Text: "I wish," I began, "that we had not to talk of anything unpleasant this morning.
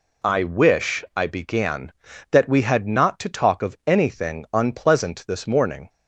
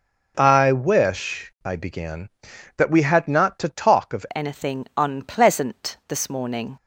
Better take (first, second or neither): first